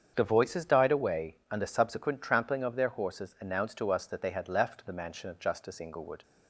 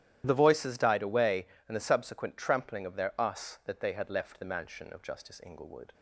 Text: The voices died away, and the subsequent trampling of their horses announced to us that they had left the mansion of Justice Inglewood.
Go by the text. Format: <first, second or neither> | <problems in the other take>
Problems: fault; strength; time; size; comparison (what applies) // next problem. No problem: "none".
first | starts louder than the rest; strong; until 1.2 s; 12 dB; strong in the first // skips "horses announced to"; at 3.1 s